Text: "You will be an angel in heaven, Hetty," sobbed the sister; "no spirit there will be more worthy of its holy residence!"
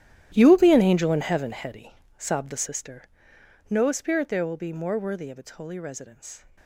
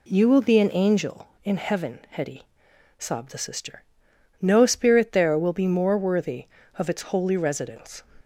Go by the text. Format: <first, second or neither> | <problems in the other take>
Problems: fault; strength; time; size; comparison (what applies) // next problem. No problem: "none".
second | gets quieter; strong; throughout; 16.5 dB